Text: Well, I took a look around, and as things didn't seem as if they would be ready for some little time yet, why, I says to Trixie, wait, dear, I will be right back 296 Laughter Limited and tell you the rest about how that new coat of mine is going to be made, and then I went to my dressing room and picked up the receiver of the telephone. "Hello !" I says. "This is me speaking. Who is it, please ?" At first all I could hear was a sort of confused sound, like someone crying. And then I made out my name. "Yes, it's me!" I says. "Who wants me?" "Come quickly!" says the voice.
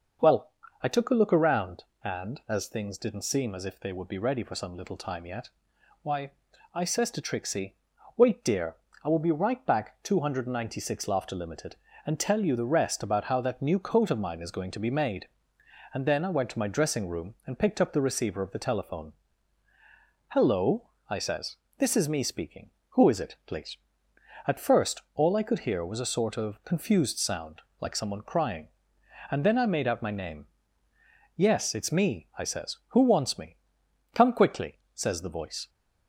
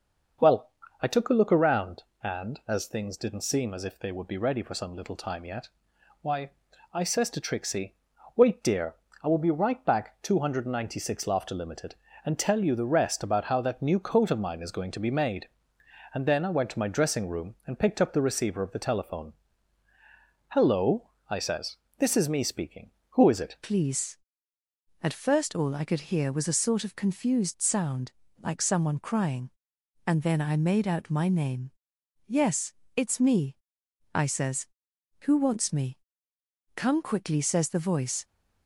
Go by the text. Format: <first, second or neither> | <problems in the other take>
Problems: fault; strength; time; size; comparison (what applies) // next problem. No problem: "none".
first | starts louder than the rest; noticeable; until 1.7 s; 6 dB; noticeable in the first // changes voice at "please"; from 23.6 s on; 14.6 s long